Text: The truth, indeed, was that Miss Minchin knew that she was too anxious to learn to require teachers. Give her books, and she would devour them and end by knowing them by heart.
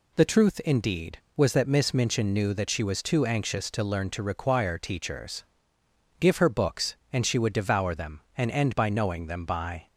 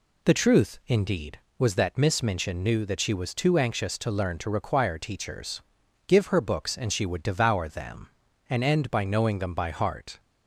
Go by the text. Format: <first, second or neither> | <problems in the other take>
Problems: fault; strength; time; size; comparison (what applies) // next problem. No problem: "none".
second | stops before "heart"; at 9.8 s